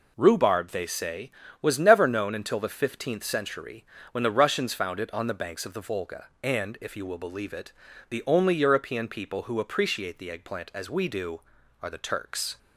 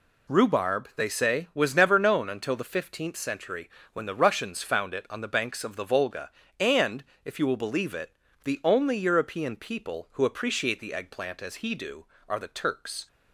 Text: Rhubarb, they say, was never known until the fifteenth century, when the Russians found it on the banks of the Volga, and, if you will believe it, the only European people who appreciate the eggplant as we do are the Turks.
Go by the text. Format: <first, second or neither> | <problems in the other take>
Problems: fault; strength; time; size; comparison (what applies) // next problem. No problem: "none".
first | says "he" for "we"; at 11.5 s